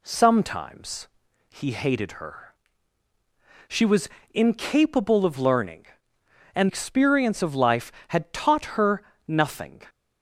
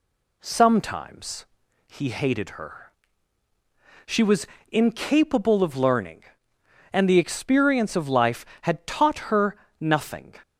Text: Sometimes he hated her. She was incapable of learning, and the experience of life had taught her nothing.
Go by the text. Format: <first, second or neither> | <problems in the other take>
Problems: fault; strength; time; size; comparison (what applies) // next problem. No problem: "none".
second | pauses between "Sometimes" and "he"; at 1.0 s; 0.40 s long; also in the second // pauses between "was" and "incapable"; slight; at 4.0 s; 0.24 s long; slight in the second // skips "the"; at 6.6 s // pauses between "her" and "nothing"; slight; at 9.0 s; 0.26 s long; slight in the second